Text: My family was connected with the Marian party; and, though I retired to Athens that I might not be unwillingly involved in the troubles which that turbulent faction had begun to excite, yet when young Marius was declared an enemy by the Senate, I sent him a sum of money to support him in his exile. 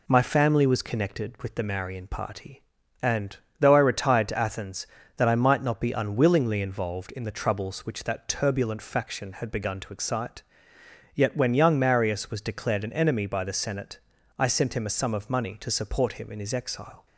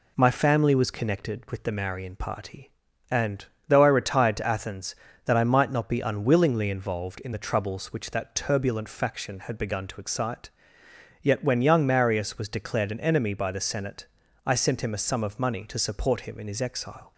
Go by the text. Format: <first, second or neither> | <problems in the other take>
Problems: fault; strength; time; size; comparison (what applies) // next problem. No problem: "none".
neither | none